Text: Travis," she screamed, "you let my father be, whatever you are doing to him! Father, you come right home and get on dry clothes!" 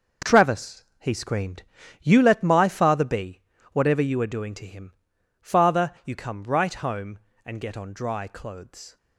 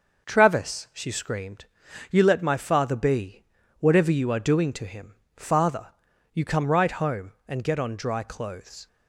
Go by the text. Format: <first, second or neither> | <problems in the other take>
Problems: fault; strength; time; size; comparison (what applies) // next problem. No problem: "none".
second | says "he" for "she"; at 0.9 s